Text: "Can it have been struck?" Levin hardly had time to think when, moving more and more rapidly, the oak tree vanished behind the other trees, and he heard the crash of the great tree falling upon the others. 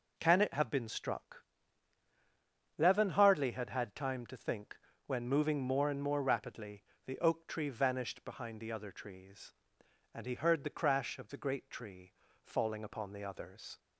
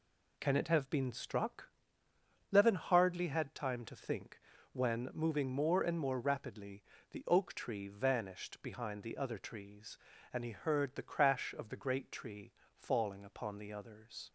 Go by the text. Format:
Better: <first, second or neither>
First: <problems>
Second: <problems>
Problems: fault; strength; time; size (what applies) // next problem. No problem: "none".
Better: second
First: says "had" twice; at 3.6 s // pauses between "think" and "when"; slight; at 4.7 s; 0.26 s long // pauses between "tree" and "falling"; slight; at 12.1 s; 0.34 s long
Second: pauses between "think" and "when"; slight; at 4.3 s; 0.34 s long // pauses between "tree" and "falling"; slight; at 12.5 s; 0.22 s long